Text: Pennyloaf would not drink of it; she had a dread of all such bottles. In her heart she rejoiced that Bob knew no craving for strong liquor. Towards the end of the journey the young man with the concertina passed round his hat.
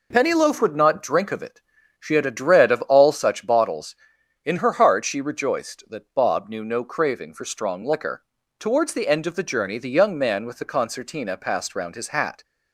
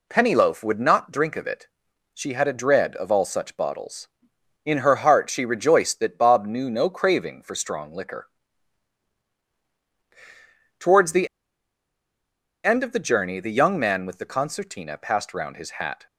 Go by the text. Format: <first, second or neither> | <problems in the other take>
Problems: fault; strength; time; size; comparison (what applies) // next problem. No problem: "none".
first | pauses between "the" and "end"; strong; at 11.2 s; 1.3 s long